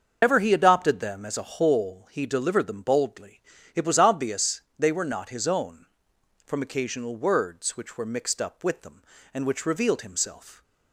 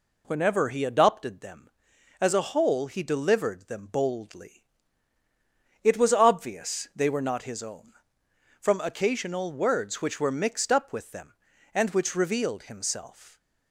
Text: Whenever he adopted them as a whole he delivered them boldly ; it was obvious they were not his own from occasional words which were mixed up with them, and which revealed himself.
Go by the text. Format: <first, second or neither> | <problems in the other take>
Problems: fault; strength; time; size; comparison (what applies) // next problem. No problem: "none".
second | loses the start of "Whenever"; at 0.2 s; 130 ms // starts louder than the rest; until 1.2 s; 6.5 dB // pauses between "obvious" and "they"; slight; at 4.6 s; 0.16 s long